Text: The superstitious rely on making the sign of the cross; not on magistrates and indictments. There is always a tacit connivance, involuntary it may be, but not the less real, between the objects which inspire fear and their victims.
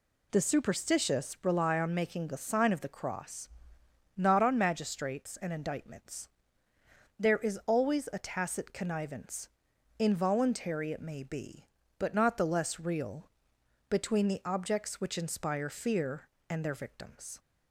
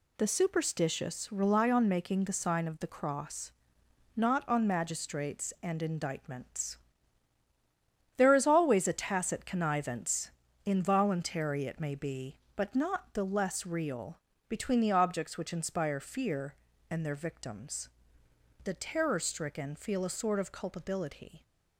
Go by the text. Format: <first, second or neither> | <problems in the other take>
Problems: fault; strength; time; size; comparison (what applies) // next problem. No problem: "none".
first | goes on to say "The terror stricken feel a sort of culpability"; strong; from 18.6 s on; 2.7 s long